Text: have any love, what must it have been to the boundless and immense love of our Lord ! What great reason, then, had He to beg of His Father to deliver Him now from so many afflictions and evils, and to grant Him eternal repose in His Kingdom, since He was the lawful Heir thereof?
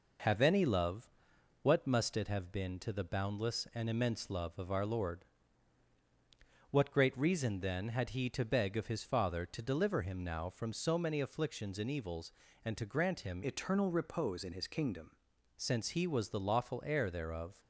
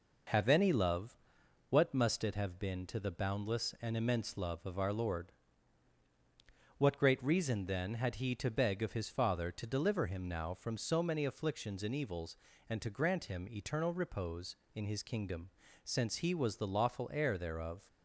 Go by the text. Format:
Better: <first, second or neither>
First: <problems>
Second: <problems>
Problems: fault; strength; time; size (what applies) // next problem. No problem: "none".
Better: second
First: changes voice from "eternal" to "Kingdom"; from 13.4 to 15.1 s; 1.7 s long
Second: none